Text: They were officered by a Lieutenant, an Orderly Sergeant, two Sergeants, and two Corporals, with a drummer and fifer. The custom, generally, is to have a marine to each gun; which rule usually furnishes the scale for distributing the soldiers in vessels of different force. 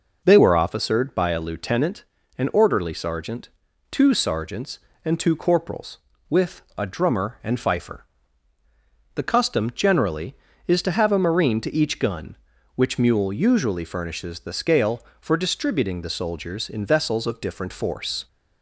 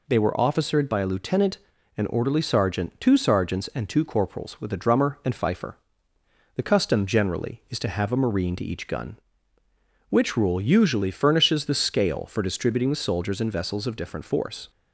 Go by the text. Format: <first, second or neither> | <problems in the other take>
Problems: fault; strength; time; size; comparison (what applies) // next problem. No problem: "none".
second | pauses between "with" and "a"; slight; at 6.6 s; 0.16 s long // says "mule" for "rule"; at 12.9 s